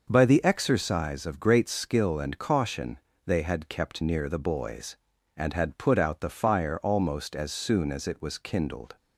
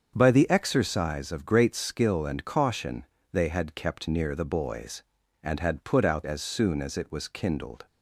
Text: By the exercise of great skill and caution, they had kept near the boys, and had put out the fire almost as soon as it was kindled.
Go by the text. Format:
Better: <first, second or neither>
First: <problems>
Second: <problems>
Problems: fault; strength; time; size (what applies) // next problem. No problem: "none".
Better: first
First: starts louder than the rest; noticeable; until 1.1 s; 6 dB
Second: starts louder than the rest; strong; until 1.1 s; 7 dB // skips "the fire almost"; at 6.2 s